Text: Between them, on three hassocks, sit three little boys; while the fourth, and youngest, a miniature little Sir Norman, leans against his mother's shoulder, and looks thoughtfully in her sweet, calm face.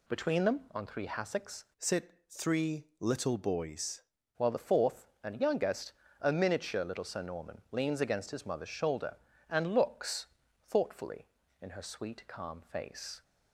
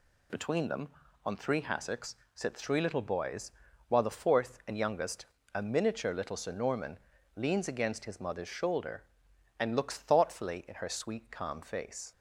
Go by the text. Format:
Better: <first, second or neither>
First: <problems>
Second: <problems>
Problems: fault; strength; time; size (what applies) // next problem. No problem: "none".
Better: second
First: changes voice from "sit" to "boys"; from 1.7 to 4.0 s; 2.3 s long // pauses between "looks" and "thoughtfully"; at 10.2 s; 0.40 s long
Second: none